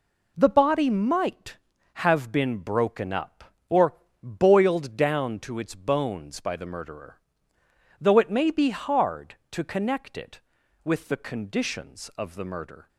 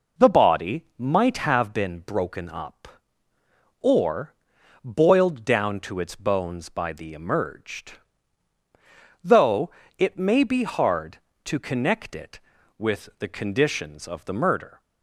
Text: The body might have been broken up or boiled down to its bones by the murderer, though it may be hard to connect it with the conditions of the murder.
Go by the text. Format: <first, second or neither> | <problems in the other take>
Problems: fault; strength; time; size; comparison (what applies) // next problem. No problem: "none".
first | pauses between "or" and "boiled"; noticeable; at 4.3 s; 0.50 s long; slight in the first // says "emerged" for "murderer"; at 7.1 s // pauses between "though" and "it"; slight; at 9.6 s; 0.28 s long